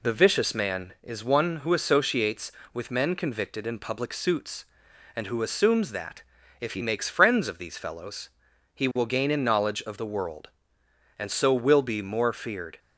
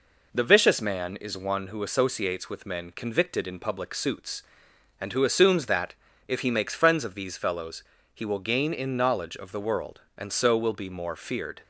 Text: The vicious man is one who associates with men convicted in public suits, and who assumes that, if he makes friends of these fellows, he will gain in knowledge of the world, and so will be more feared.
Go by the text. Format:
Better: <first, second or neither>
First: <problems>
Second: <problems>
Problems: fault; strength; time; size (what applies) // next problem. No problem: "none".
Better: neither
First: none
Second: none